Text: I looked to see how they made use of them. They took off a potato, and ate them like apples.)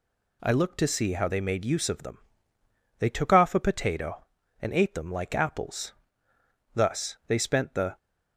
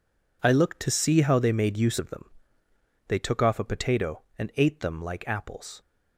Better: second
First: goes on to say "Thus they spent the"; noticeable; from 6.7 s on; 1.2 s long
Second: none

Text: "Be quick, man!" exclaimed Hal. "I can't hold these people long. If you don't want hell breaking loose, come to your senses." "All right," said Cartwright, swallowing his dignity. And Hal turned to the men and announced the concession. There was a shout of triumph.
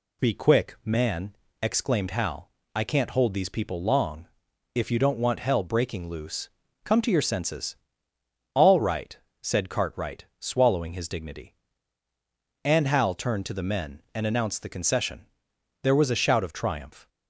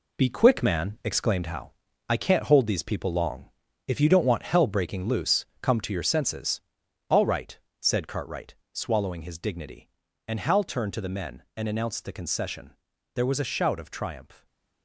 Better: first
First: none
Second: gets quieter; throughout; 6.5 dB // stays silent after the last word; slight; from 14.3 s on; 0.5 s long

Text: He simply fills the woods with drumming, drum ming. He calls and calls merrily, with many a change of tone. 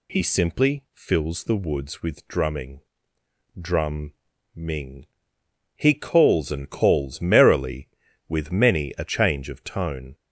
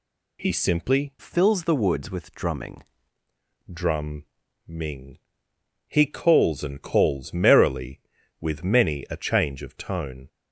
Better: first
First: pauses between "drum" and "ming"; at 4.1 s; 0.42 s long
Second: changes voice from "fills" to "drumming"; from 1.1 to 2.8 s; 1.7 s long // pauses between "drum" and "ming"; at 4.2 s; 0.42 s long

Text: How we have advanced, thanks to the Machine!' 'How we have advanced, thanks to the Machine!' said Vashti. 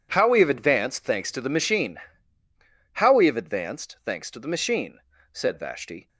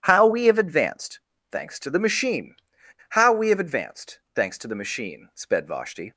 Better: first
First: none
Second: starts louder than the rest; strong; until 1.0 s; 10.5 dB // says "sped" for "said"; at 5.3 s

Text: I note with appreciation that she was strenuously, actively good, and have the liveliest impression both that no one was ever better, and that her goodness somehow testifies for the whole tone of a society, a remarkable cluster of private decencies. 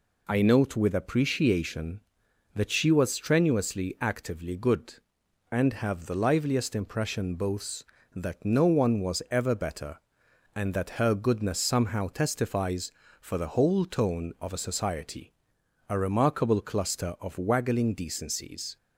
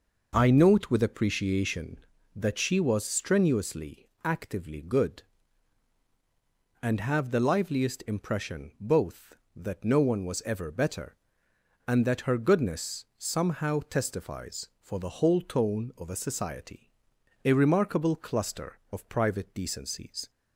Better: second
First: says "waggling" for "private"; at 17.3 s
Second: none

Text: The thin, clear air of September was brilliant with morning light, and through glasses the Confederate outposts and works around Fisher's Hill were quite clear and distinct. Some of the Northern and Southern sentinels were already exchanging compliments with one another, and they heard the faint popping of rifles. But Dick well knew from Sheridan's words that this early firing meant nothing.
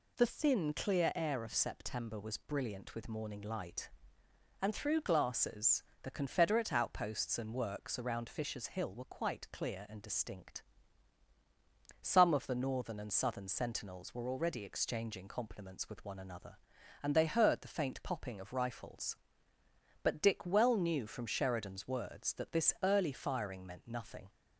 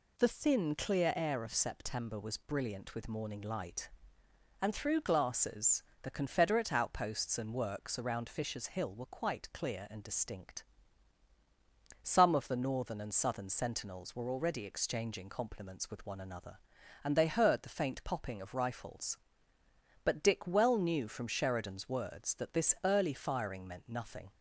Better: neither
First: pauses between "glasses" and "the"; slight; at 5.8 s; 0.20 s long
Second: pauses between "glasses" and "the"; slight; at 5.8 s; 0.20 s long

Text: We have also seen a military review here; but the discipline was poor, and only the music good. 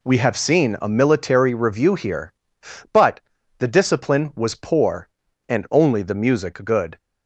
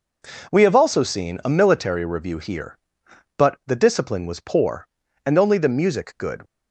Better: second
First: skips "also"; at 0.3 s // pauses between "but" and "the"; at 3.2 s; 0.38 s long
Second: none

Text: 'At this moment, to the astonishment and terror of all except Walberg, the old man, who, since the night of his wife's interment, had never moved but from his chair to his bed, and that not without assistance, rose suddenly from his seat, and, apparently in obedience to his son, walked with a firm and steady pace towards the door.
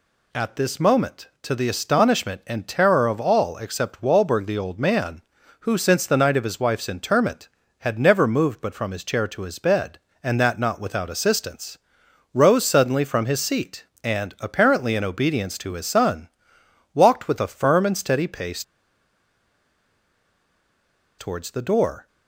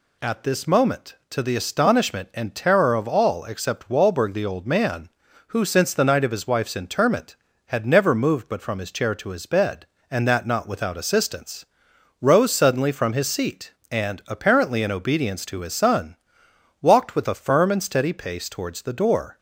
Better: second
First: pauses between "pace" and "towards"; strong; at 18.6 s; 2.5 s long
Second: none

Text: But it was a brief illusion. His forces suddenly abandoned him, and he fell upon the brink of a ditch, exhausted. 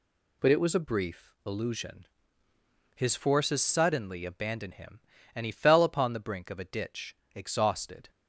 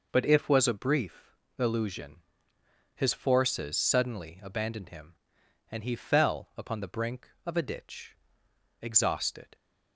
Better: first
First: none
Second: says "if" for "it"; at 0.2 s // pauses between "brief" and "illusion"; slight; at 1.3 s; 0.24 s long

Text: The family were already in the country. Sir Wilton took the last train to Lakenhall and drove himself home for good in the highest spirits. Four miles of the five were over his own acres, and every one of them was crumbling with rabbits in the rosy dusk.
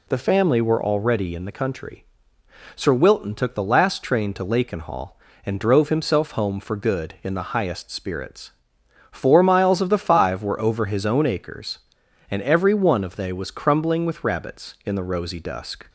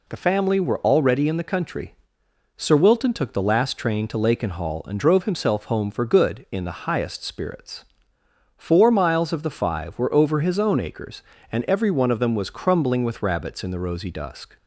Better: second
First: says "they" for "them"; at 13.1 s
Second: none

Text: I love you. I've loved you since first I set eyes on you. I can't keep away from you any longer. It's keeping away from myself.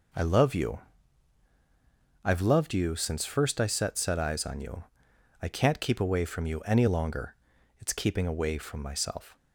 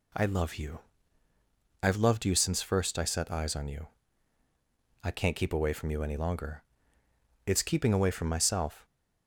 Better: second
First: says "set" twice; at 3.9 s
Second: none

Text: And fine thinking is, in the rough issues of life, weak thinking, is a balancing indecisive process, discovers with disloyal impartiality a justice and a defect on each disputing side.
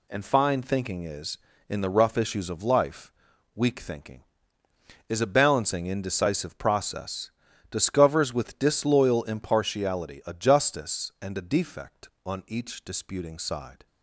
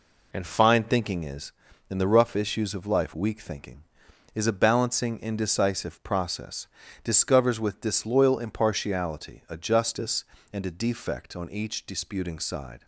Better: neither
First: none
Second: none

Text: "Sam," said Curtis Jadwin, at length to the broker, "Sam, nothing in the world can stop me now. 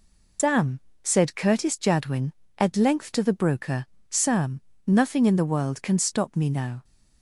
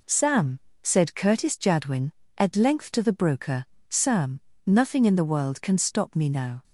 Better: second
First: loses the start of "Sam"; at 0.3 s; 140 ms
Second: none

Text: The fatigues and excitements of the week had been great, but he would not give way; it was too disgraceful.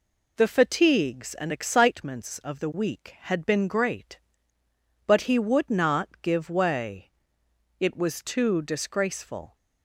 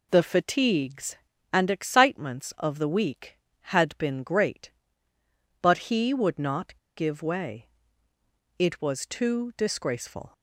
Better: first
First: none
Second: pauses between "not" and "give"; slight; at 6.7 s; 0.23 s long

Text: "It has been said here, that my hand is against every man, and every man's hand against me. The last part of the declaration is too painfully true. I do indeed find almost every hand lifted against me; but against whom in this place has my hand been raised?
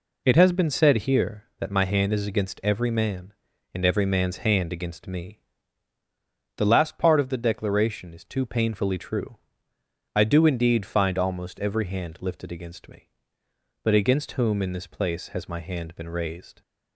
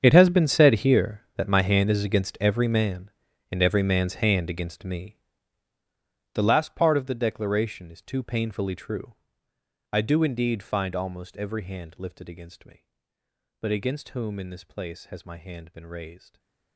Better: first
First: none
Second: gets quieter; strong; throughout; 18 dB // stays silent after the last word; slight; from 16.1 s on; 0.6 s long

